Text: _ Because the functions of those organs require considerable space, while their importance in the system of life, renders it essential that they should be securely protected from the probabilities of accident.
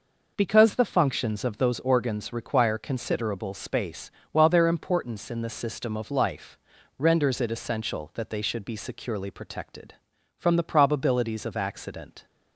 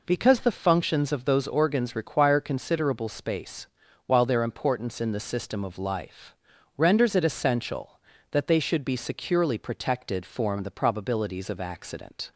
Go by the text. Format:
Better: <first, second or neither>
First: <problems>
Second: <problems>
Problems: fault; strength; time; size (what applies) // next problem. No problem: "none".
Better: first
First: none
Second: says "form" for "from"; at 10.2 s